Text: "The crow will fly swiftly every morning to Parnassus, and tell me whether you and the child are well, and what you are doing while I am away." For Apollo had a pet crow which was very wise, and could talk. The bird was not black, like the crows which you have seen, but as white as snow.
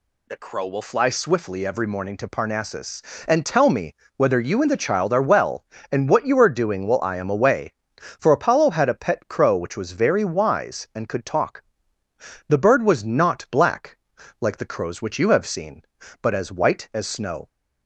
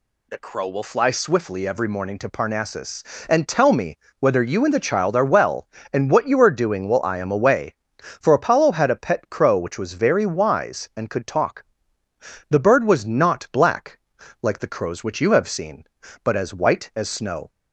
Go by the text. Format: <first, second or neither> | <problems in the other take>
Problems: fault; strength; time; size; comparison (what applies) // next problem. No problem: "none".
neither | pauses between "me" and "whether"; slight; the same in both